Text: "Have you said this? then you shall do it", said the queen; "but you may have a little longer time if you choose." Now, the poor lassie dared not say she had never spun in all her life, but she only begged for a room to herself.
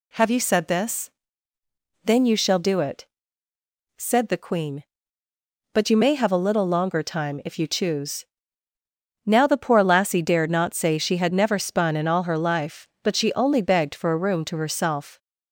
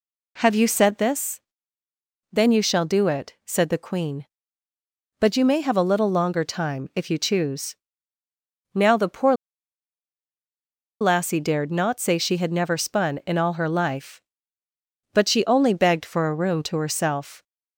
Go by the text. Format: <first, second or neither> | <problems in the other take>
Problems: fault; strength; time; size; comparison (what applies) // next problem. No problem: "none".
first | pauses between "poor" and "lassie"; strong; at 9.3 s; 1.6 s long